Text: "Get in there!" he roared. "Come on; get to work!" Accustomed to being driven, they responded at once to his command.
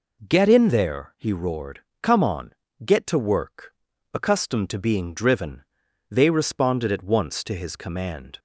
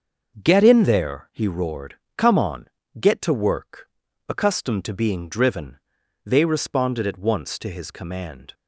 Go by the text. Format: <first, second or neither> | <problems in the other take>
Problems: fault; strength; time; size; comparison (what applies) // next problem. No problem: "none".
first | gets quieter; strong; throughout; 7 dB